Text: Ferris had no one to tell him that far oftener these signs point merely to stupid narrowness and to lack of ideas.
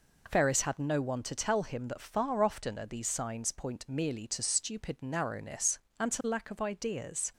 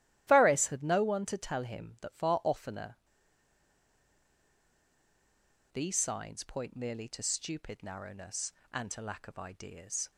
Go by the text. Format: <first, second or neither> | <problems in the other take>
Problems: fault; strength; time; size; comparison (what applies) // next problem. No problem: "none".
first | starts louder than the rest; strong; until 1.2 s; 14 dB // pauses between "oftener" and "these"; strong; at 2.9 s; 2.7 s long